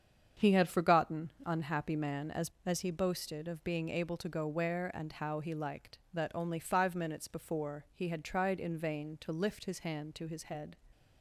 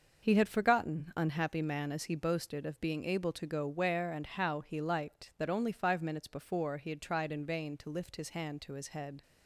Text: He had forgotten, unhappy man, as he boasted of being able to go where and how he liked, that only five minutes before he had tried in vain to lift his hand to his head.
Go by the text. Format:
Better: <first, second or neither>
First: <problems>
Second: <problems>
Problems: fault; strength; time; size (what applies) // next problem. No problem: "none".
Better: second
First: starts louder than the rest; strong; until 1.5 s; 7.5 dB // says "as" twice; at 2.6 s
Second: starts louder than the rest; noticeable; until 1.3 s; 6 dB